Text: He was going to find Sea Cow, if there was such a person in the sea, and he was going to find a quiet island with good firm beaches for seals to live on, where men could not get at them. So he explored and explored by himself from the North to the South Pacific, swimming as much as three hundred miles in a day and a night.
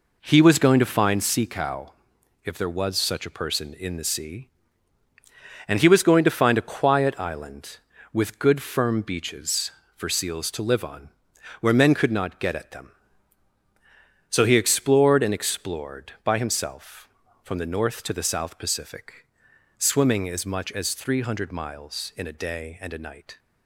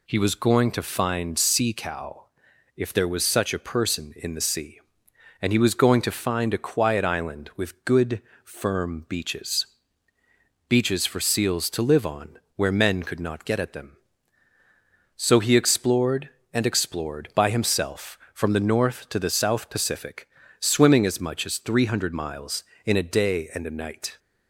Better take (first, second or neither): first